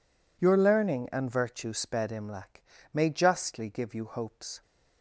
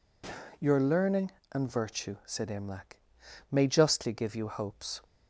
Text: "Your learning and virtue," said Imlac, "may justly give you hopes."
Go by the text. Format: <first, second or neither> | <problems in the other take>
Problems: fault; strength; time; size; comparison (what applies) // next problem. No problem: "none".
second | says "sped" for "said"; at 1.7 s